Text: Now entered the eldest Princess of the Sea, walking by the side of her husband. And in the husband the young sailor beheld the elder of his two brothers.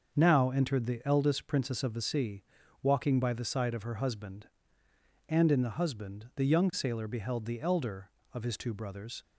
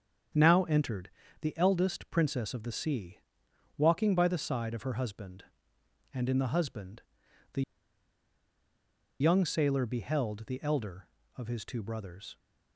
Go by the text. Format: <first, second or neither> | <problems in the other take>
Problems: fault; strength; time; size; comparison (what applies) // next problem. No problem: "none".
first | starts louder than the rest; strong; until 1.7 s; 8 dB; also in the first // pauses between "entered" and "the"; slight; at 1.1 s; 0.32 s long // pauses between "husband" and "the"; noticeable; at 7.0 s; 0.50 s long // pauses between "the" and "young"; strong; at 7.6 s; 1.5 s long